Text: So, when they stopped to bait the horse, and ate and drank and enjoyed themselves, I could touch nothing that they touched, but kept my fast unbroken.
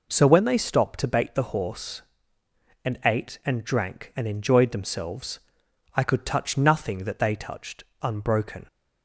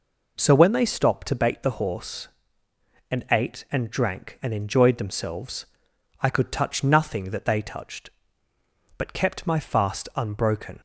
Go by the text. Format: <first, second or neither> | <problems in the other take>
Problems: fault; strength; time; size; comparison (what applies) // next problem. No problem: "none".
second | skips "but kept my fast"; at 7.9 s